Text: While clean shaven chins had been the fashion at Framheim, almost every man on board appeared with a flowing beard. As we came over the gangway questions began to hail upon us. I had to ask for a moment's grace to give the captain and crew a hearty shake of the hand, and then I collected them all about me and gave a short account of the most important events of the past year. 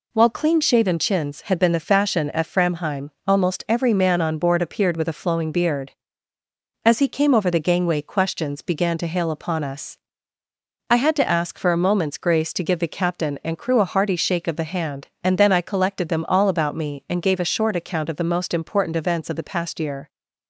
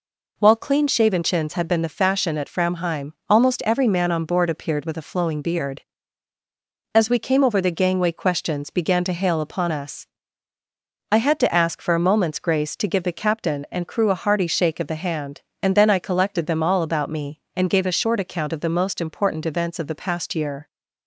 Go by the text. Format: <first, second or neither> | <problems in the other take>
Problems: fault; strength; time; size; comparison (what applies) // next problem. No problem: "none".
second | says "he" for "we"; at 6.9 s